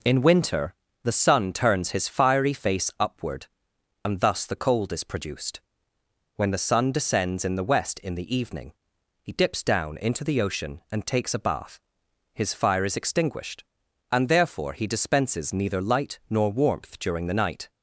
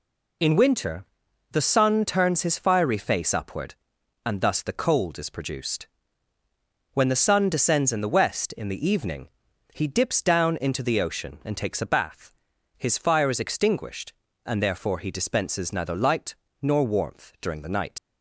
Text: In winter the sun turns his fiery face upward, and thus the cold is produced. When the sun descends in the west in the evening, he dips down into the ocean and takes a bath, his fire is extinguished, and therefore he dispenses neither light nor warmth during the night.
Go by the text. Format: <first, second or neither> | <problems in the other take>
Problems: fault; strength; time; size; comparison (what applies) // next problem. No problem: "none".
first | pauses between "winter" and "the"; noticeable; at 1.0 s; 0.46 s long; slight in the first // pauses between "light" and "nor"; slight; at 16.3 s; 0.26 s long // leaves "night" unfinished; at 17.9 s; 70 ms